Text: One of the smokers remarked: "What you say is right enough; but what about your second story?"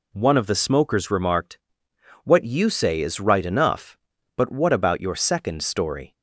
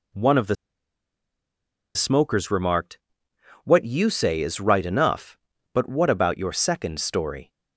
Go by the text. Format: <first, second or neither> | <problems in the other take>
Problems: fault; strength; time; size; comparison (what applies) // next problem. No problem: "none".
first | pauses between "the" and "smokers"; strong; at 0.5 s; 1.4 s long